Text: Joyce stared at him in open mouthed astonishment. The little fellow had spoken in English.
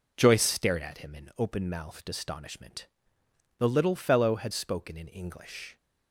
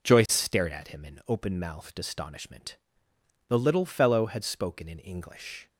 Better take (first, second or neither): neither